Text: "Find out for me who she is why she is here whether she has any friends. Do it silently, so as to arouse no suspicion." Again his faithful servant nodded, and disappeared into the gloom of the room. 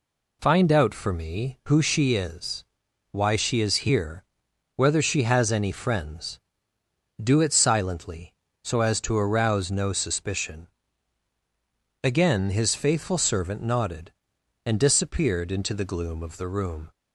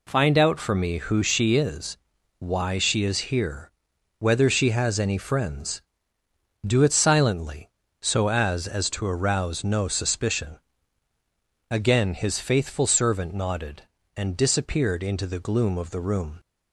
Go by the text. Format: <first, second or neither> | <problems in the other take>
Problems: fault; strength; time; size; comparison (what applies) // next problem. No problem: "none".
first | pauses between "is" and "why"; at 1.9 s; 0.40 s long; noticeable in the first // pauses between "here" and "whether"; noticeable; at 3.6 s; 0.50 s long; noticeable in the first // says "as" twice; at 8.6 s